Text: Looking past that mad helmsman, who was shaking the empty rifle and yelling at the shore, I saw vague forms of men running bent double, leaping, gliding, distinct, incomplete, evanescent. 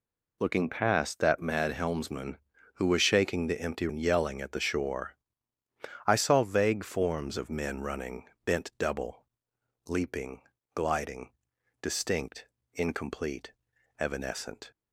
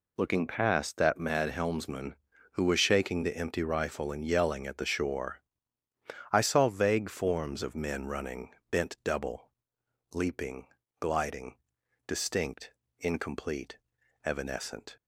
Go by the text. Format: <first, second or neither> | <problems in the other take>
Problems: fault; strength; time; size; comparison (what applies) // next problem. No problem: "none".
second | skips "rifle"; at 3.8 s // pauses between "running" and "bent"; slight; at 8.2 s; 0.20 s long; slight in the second